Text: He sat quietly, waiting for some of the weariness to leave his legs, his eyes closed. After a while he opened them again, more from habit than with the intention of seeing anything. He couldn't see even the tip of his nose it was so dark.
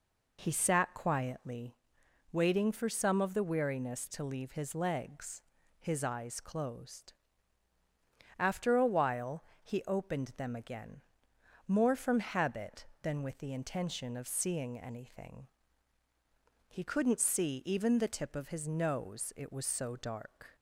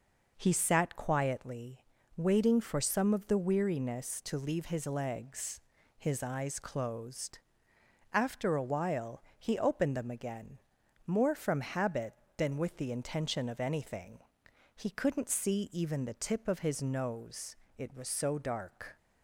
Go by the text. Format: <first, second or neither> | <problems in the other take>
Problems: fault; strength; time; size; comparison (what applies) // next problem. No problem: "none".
first | pauses between "while" and "he"; slight; at 9.2 s; 0.16 s long; slight in the first // skips "seeing"; at 13.6 s // pauses between "nose" and "it"; slight; at 17.5 s; 0.22 s long